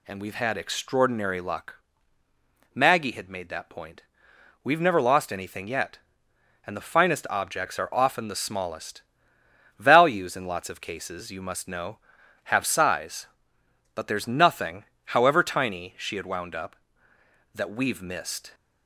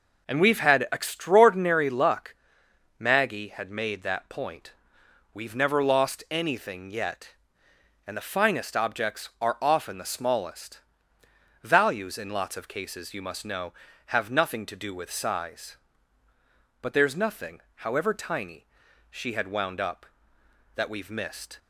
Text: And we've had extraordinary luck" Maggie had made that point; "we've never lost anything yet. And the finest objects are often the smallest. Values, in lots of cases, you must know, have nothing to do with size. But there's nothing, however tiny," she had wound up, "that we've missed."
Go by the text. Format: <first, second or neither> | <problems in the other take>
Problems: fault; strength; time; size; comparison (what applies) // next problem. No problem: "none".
second | pauses between "luck" and "Maggie"; noticeable; at 1.7 s; 0.98 s long; noticeable in the second // skips "nothing to do with"; at 12.6 s